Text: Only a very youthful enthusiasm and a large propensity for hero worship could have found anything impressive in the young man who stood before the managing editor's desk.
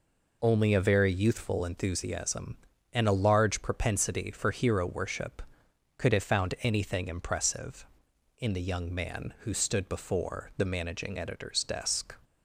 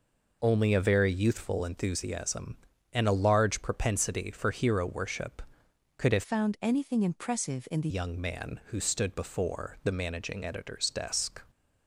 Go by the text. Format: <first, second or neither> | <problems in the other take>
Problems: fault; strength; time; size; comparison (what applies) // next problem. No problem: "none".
first | changes voice from "found" to "the"; from 6.2 to 7.8 s; 1.6 s long